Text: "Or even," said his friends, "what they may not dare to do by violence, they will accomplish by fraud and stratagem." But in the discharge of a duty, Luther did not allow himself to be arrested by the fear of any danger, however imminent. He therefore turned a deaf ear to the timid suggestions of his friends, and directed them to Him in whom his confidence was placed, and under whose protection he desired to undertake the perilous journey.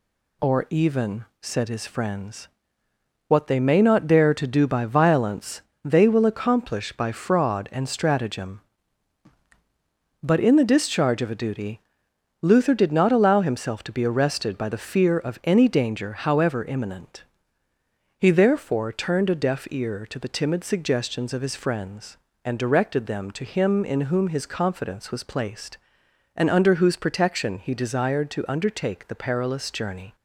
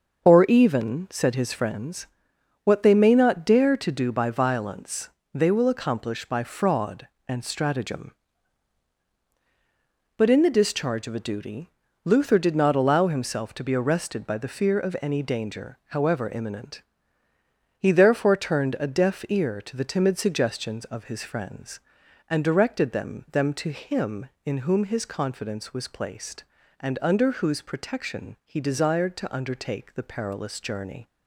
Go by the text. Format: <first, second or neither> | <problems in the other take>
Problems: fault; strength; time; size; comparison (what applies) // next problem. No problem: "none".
first | starts louder than the rest; until 1.2 s; 6.5 dB // says "them" twice; at 23.3 s